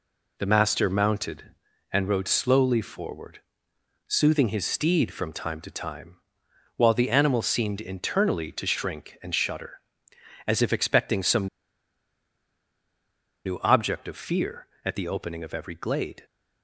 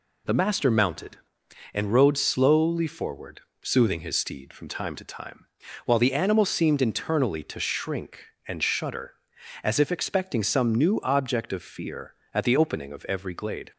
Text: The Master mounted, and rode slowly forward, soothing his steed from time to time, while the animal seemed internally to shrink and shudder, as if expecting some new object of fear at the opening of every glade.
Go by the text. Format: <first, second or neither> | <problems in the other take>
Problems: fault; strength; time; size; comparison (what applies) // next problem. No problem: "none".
second | pauses between "some" and "new"; strong; at 11.4 s; 1.9 s long